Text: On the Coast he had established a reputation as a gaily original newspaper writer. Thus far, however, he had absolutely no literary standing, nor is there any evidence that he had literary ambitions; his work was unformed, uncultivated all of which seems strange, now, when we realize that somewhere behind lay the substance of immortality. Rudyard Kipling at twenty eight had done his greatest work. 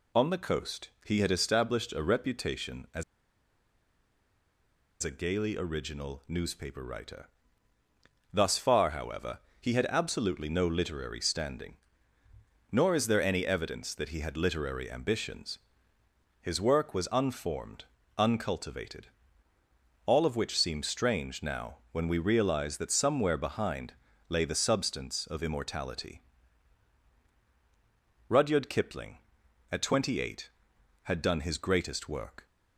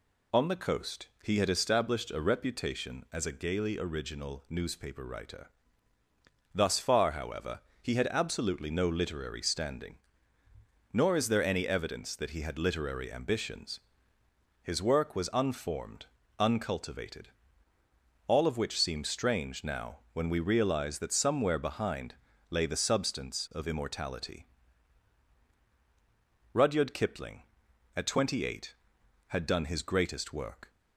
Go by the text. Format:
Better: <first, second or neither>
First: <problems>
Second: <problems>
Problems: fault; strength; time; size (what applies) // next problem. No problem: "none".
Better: second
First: pauses between "Coast" and "he"; slight; at 0.8 s; 0.16 s long // pauses between "as" and "a"; strong; at 3.0 s; 1.9 s long // pauses between "uncultivated" and "all"; at 19.0 s; 1.0 s long // pauses between "behind" and "lay"; at 23.9 s; 0.38 s long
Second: pauses between "Coast" and "he"; slight; at 1.0 s; 0.16 s long // pauses between "uncultivated" and "all"; at 17.2 s; 1.0 s long // pauses between "behind" and "lay"; at 22.1 s; 0.38 s long